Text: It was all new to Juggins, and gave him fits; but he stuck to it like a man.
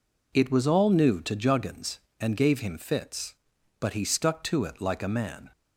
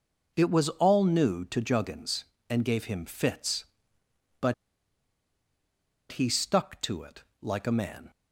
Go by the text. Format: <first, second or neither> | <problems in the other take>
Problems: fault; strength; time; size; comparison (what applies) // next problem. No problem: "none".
first | pauses between "but" and "he"; strong; at 4.5 s; 1.5 s long // pauses between "it" and "like"; slight; at 7.2 s; 0.18 s long